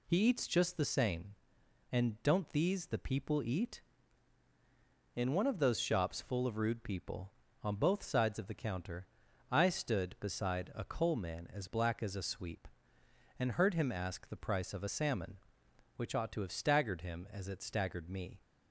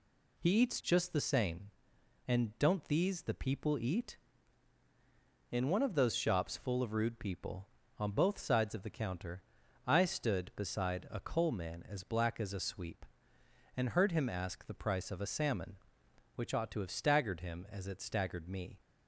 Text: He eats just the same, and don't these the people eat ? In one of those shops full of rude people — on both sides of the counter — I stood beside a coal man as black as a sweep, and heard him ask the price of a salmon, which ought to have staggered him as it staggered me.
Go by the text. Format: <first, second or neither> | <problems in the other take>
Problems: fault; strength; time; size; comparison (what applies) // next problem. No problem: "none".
neither | none